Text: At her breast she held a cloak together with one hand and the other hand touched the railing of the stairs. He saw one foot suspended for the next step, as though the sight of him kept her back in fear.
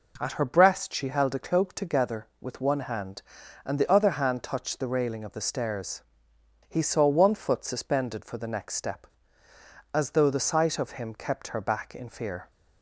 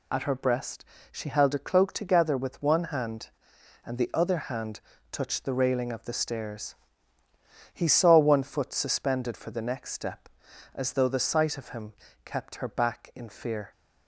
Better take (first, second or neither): first